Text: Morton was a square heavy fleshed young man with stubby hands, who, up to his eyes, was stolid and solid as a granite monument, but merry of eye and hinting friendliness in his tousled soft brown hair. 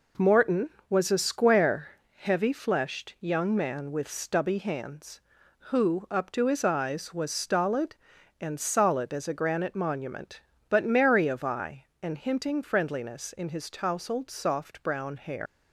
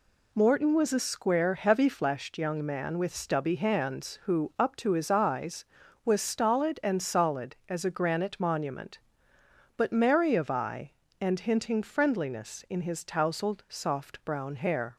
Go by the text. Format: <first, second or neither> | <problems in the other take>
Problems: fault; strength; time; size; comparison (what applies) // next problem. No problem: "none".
second | pauses between "square" and "heavy"; slight; at 1.8 s; 0.28 s long // leaves "hair" unfinished; at 15.4 s; 120 ms